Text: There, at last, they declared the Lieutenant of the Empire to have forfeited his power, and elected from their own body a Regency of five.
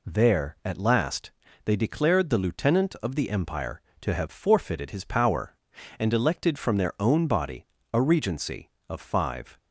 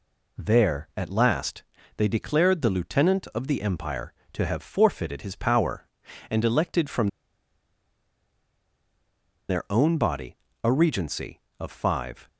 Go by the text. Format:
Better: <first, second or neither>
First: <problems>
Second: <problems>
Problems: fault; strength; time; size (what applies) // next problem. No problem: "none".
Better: first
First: pauses between "body" and "a"; slight; at 7.6 s; 0.28 s long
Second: pauses between "from" and "their"; strong; at 7.0 s; 2.4 s long // pauses between "body" and "a"; slight; at 10.3 s; 0.28 s long